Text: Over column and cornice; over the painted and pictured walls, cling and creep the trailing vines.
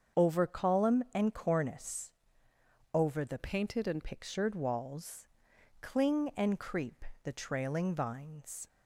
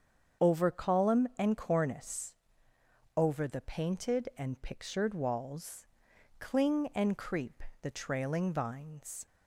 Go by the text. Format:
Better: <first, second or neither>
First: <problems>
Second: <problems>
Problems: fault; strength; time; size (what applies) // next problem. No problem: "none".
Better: second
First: starts louder than the rest; until 1.2 s; 7 dB // changes voice from "painted" to "and"; from 3.3 to 4.0 s; 0.7 s long // pauses between "creep" and "the"; slight; at 7.0 s; 0.20 s long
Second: starts louder than the rest; strong; until 1.5 s; 7.5 dB // pauses between "creep" and "the"; slight; at 7.6 s; 0.20 s long